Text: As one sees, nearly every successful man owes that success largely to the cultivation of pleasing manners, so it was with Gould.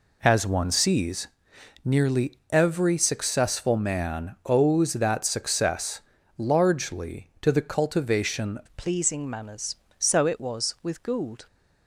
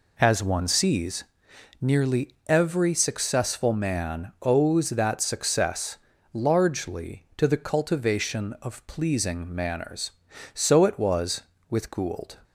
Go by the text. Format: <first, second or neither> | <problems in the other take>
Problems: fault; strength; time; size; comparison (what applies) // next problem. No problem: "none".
second | pauses between "nearly" and "every"; slight; at 2.3 s; 0.16 s long; slight in the second // pauses between "success" and "largely"; slight; at 6.0 s; 0.34 s long; slight in the second // changes voice at "of"; from 8.6 s on; 2.8 s long